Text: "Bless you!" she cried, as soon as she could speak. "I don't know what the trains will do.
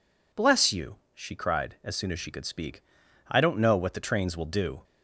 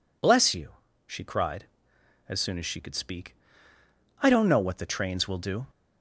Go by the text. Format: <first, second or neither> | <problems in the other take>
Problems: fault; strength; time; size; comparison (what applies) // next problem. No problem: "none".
neither | none